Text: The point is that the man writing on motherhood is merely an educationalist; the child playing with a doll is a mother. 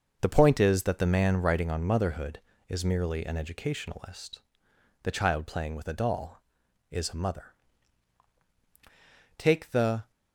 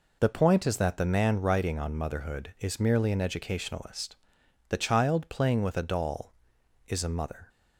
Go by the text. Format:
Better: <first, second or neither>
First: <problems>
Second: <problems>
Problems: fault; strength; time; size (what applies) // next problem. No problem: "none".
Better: second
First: starts louder than the rest; noticeable; until 1.2 s; 6 dB // goes on to say "Take the"; noticeable; from 9.3 s on; 0.72 s long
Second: none